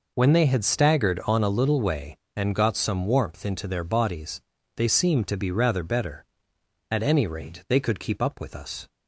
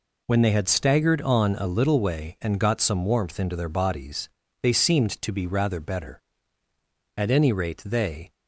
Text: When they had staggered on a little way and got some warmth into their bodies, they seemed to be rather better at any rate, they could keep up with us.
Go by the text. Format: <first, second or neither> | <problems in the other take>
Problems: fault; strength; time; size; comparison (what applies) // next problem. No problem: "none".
first | stops before "could keep up with us"; at 8.3 s